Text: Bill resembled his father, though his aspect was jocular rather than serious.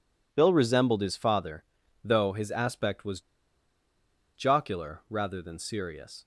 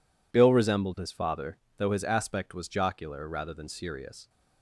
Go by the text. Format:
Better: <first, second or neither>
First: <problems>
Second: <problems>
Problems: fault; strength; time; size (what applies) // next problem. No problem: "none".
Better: second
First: pauses between "was" and "jocular"; at 3.1 s; 1.1 s long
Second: none